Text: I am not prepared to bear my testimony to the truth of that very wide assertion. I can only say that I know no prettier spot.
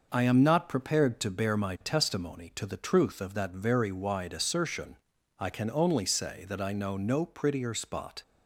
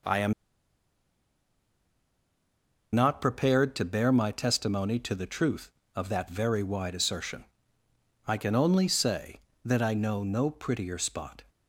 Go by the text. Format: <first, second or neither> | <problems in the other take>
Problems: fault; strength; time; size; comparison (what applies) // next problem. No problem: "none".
first | pauses between "am" and "not"; strong; at 0.3 s; 2.6 s long